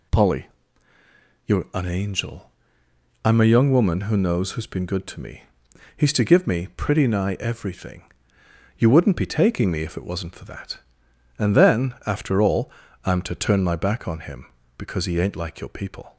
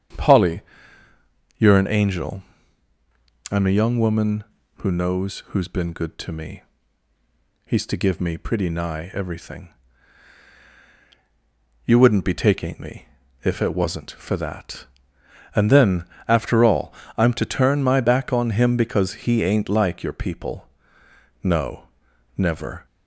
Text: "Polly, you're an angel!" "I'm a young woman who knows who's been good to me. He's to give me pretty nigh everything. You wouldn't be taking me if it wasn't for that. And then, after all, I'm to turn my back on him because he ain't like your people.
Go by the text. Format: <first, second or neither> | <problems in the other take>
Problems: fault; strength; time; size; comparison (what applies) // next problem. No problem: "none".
first | starts louder than the rest; strong; until 2.1 s; 8 dB // pauses between "me" and "if"; at 13.0 s; 0.38 s long // goes on to say "No never"; from 21.4 s on; 1.4 s long